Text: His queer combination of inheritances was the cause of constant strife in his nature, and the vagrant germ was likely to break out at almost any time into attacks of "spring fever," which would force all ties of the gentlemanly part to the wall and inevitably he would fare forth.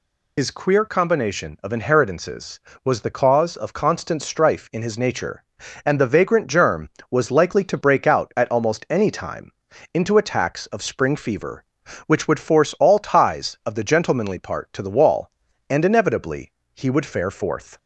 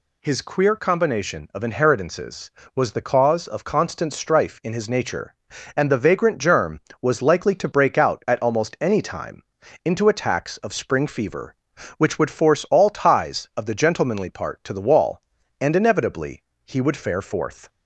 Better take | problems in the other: second | loses the start of "His"; at 0.3 s; 70 ms // pauses between "time" and "into"; at 9.5 s; 0.42 s long; also in the second // pauses between "inevitably" and "he"; slight; at 16.5 s; 0.22 s long; slight in the second

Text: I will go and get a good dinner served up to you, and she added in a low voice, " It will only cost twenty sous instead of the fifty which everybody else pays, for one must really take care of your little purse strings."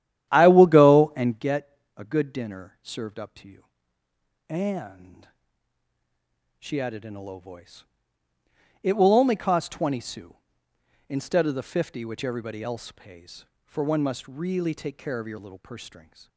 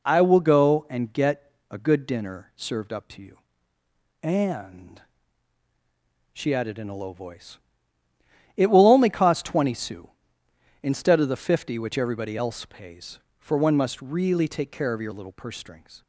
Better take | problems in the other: second | starts louder than the rest; strong; until 1.5 s; 11.5 dB // pauses between "get" and "a"; slight; at 1.7 s; 0.18 s long; slight in the second // pauses between "and" and "she"; strong; at 5.2 s; 1.3 s long; strong in the second

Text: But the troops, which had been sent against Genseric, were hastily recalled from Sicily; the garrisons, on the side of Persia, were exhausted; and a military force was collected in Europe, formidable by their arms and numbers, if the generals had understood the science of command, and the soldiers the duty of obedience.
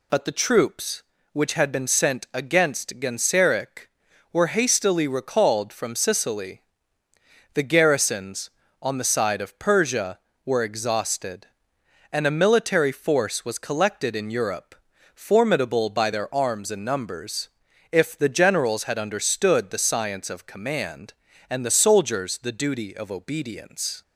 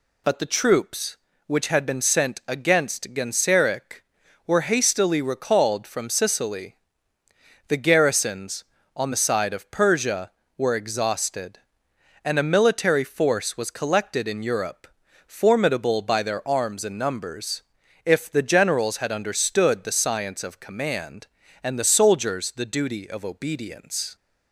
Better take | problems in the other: neither | none

